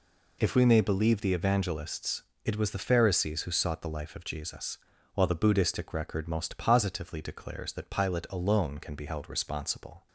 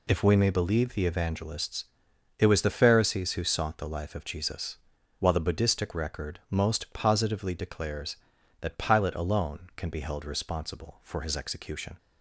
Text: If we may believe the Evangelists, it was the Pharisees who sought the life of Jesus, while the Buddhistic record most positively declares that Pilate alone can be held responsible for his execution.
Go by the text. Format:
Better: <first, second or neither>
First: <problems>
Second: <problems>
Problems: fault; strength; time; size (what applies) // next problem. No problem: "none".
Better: second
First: stops before "for his execution"; at 10.0 s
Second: none